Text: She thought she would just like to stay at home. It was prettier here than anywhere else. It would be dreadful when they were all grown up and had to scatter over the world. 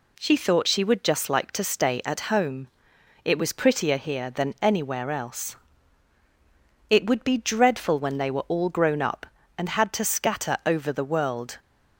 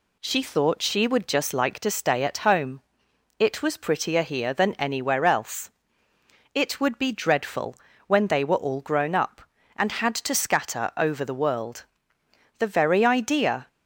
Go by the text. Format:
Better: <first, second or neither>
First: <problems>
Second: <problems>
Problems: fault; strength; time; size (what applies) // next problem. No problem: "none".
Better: first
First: none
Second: pauses between "dreadful" and "when"; slight; at 7.7 s; 0.32 s long // goes on to say "The very idea"; noticeable; from 12.5 s on; 1.1 s long